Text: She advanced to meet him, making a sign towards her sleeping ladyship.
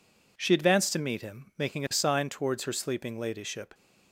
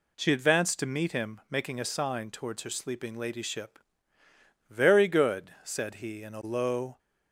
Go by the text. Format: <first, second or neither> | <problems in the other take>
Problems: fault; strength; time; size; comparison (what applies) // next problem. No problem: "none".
first | goes on to say "Very good said he in a low"; strong; from 4.7 s on; 2.2 s long